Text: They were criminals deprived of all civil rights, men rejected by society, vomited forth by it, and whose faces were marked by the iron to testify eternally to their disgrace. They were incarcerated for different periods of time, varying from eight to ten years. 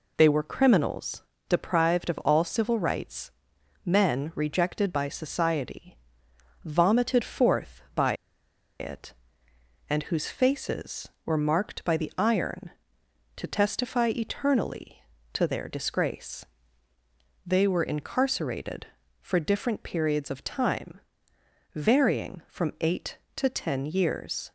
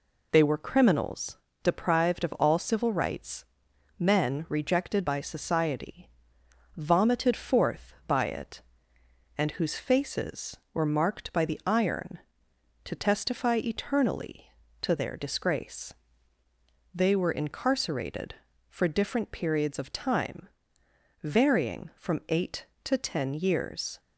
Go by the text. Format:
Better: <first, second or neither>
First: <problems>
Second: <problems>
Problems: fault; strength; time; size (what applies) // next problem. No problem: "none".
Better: second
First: pauses between "criminals" and "deprived"; slight; at 1.2 s; 0.24 s long // pauses between "by" and "it"; noticeable; at 8.1 s; 0.66 s long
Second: pauses between "criminals" and "deprived"; slight; at 1.3 s; 0.24 s long